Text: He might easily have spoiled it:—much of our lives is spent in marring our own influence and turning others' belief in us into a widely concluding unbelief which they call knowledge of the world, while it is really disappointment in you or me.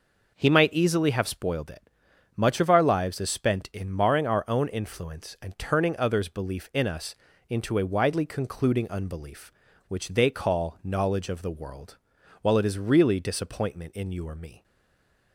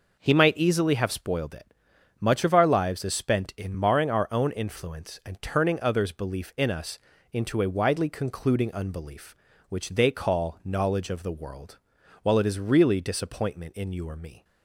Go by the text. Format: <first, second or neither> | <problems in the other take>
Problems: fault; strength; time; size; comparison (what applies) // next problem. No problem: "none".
second | pauses between "us" and "into"; slight; at 7.1 s; 0.34 s long; slight in the second // stays silent after the last word; slight; from 14.6 s on; 0.7 s long